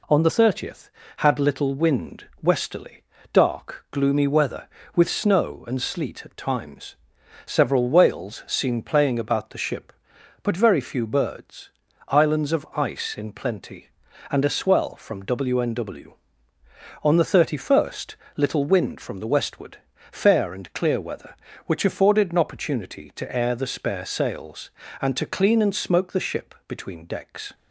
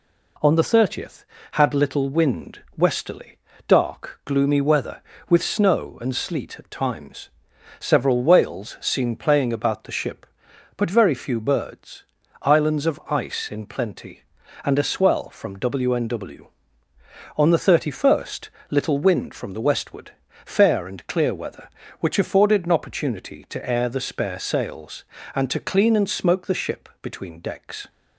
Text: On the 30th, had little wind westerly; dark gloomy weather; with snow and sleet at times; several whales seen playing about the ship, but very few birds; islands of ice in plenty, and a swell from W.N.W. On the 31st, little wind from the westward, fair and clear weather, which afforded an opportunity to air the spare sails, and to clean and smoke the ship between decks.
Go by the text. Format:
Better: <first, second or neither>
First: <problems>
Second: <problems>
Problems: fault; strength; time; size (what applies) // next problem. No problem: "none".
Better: neither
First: pauses between "wind" and "westerly"; slight; at 2.2 s; 0.16 s long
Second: pauses between "wind" and "westerly"; slight; at 2.6 s; 0.16 s long